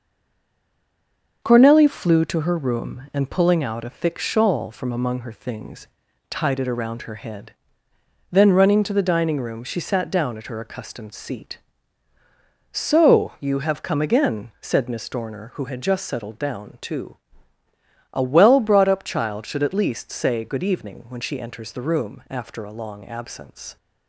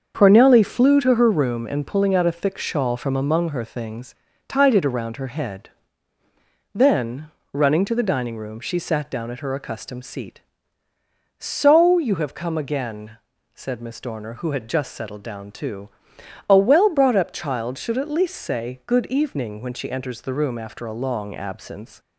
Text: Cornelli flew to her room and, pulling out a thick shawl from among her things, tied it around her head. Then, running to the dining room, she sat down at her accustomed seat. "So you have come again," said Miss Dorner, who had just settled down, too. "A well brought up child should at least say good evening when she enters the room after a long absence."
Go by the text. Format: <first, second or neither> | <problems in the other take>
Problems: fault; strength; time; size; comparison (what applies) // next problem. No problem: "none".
second | stays silent before the first word; noticeable; until 1.4 s; 1.4 s long // starts louder than the rest; until 2.4 s; 6.5 dB; also in the second